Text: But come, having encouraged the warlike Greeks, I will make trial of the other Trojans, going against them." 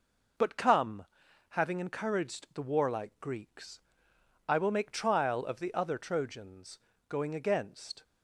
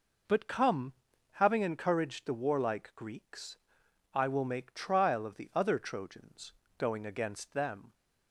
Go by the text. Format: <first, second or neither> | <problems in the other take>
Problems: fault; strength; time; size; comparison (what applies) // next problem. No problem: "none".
second | stops before "them"; at 8.0 s